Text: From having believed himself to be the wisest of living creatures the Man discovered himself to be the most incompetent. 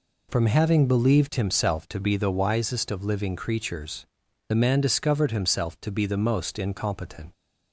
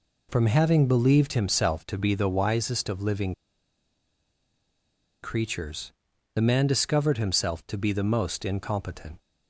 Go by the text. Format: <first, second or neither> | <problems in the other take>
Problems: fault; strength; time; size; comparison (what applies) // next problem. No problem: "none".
first | pauses between "living" and "creatures"; strong; at 3.3 s; 1.8 s long // pauses between "creatures" and "the"; at 5.9 s; 0.42 s long; also in the first